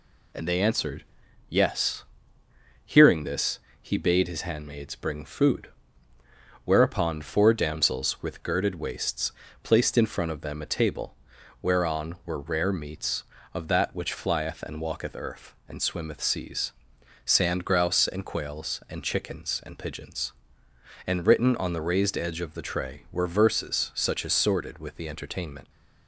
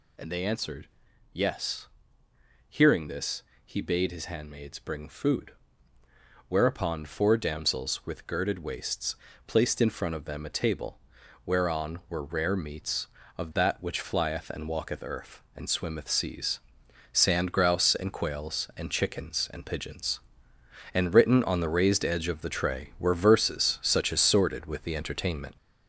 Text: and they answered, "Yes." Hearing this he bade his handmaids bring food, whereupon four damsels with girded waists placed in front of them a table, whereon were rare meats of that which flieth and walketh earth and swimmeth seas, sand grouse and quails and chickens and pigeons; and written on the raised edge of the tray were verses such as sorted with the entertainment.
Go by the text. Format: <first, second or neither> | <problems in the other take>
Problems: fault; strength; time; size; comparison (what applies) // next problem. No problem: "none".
first | gets louder; noticeable; throughout; 6 dB // pauses between "this" and "he"; slight; at 3.4 s; 0.22 s long; slight in the first // pauses between "waists" and "placed"; slight; at 9.1 s; 0.30 s long; slight in the first